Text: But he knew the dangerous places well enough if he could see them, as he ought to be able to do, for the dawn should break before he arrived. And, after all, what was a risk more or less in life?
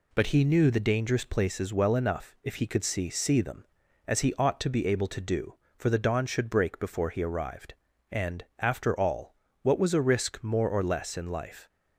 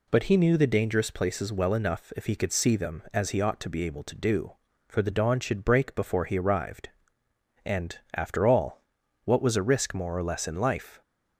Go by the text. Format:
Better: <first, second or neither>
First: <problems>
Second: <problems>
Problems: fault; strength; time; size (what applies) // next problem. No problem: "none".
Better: second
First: says "see" twice; at 3.0 s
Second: none